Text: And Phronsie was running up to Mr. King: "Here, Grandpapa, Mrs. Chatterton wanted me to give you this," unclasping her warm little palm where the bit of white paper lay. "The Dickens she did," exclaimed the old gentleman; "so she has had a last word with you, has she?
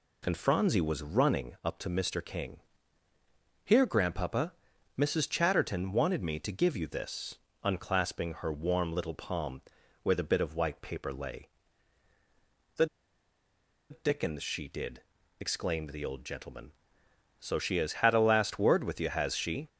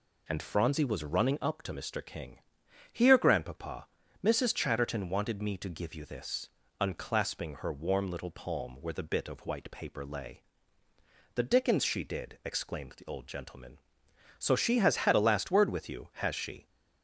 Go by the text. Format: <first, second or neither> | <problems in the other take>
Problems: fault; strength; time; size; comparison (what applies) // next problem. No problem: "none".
second | pauses between "palm" and "where"; at 9.5 s; 0.42 s long // pauses between "The" and "Dickens"; at 12.8 s; 1.0 s long